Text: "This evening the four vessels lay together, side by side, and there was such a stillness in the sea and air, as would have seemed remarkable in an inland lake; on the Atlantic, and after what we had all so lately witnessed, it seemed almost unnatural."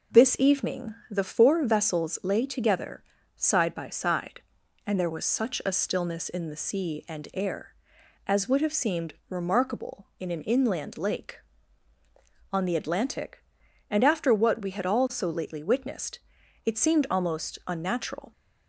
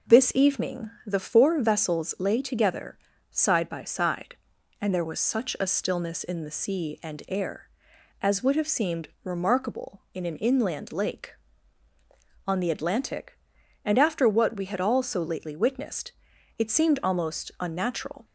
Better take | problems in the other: neither | pauses between "evening" and "the"; slight; the same in both

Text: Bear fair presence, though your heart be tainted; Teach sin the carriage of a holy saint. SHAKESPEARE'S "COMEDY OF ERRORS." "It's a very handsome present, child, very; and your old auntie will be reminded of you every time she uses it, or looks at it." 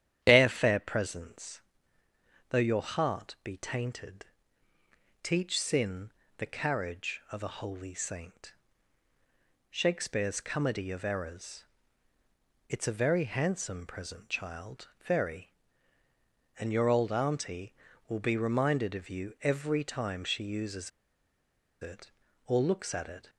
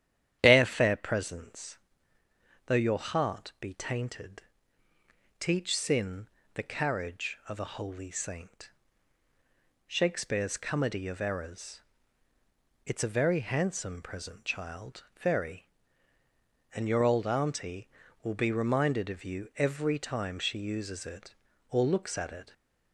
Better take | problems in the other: second | starts louder than the rest; strong; until 1.2 s; 10.5 dB; strong in the second // pauses between "sin" and "the"; slight; at 6.1 s; 0.24 s long; slight in the second // pauses between "uses" and "it"; noticeable; at 20.9 s; 0.93 s long

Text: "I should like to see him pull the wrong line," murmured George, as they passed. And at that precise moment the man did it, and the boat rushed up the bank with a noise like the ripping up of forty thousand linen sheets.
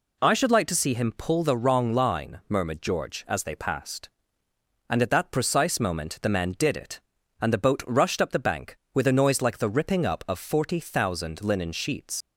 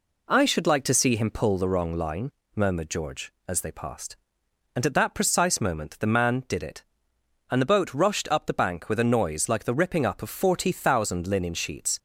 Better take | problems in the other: second | leaves "sheets" unfinished; at 12.2 s; 75 ms

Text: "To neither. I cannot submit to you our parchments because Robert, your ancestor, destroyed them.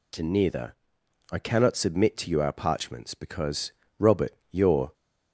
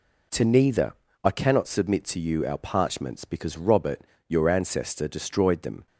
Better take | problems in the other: second | pauses between "because" and "Robert"; slight; at 3.7 s; 0.28 s long // stops before "ancestor destroyed them"; at 4.9 s

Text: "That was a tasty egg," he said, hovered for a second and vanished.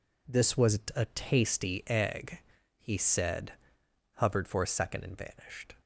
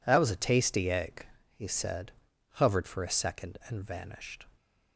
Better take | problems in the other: second | says "This" for "That"; at 0.2 s // pauses between "was" and "a"; slight; at 0.8 s; 0.16 s long

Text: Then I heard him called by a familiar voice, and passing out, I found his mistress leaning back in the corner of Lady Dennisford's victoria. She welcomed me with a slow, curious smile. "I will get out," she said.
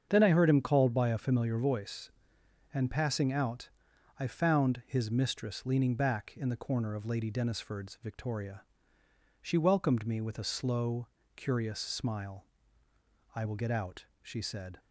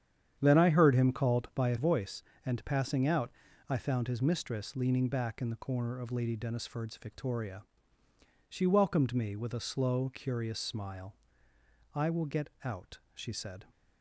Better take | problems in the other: first | starts louder than the rest; strong; until 1.4 s; 9 dB; strong in the first // skips "familiar"; at 1.7 s // pauses between "get" and "out"; slight; at 12.4 s; 0.16 s long

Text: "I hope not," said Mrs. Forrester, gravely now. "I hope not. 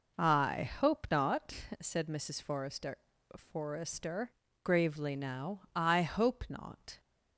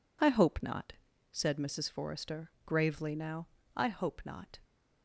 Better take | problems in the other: second | says "Forrester" twice; at 3.3 s

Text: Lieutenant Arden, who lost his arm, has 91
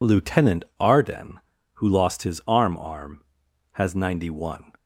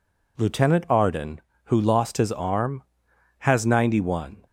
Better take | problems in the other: second | pauses between "Lieutenant" and "Arden"; slight; at 0.6 s; 0.16 s long // says "arm" twice; at 2.7 s

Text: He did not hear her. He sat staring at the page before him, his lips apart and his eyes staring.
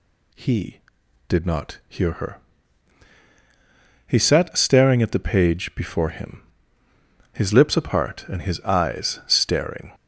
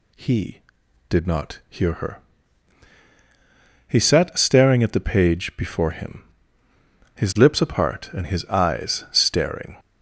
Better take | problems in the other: neither | none

